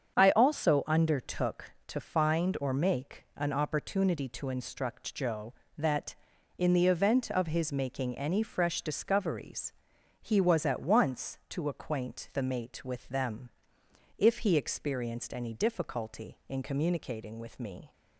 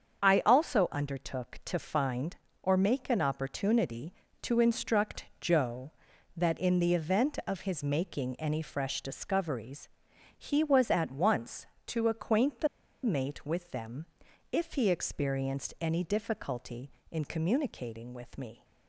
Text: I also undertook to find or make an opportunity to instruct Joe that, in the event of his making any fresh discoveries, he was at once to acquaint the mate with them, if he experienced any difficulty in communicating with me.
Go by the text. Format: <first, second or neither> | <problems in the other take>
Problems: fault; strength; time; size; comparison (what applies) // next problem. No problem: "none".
first | starts louder than the rest; until 1.2 s; 7 dB; strong in the first // pauses between "the" and "mate"; at 12.6 s; 0.36 s long